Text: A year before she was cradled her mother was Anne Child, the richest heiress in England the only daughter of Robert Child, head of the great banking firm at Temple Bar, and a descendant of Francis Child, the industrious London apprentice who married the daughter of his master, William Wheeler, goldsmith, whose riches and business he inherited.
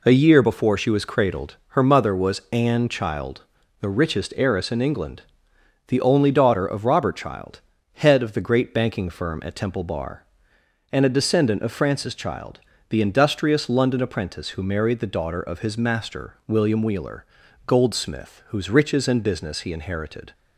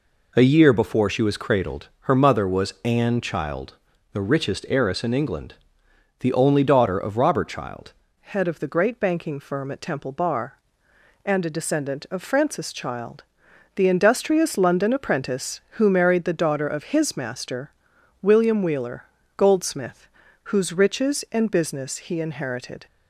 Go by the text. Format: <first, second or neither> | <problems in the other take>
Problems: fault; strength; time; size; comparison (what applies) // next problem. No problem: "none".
first | pauses between "England" and "the"; noticeable; at 5.5 s; 0.68 s long; noticeable in the first // changes voice at "head"; from 8.2 s on; 14.6 s long